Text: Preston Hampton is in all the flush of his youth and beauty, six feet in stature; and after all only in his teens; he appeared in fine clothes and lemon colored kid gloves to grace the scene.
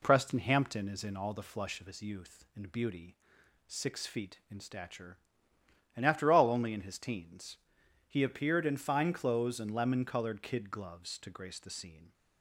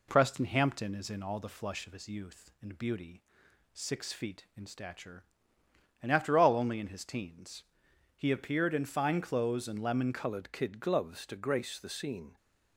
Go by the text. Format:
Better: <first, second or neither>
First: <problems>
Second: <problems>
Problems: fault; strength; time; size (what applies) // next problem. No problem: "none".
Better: first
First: none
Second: changes voice at "colored"; from 10.1 s on; 2.2 s long